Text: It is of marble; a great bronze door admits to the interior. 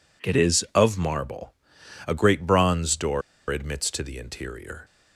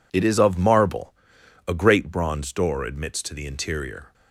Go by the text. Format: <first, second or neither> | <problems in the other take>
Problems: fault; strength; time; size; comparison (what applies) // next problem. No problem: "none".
second | pauses between "door" and "admits"; slight; at 3.2 s; 0.28 s long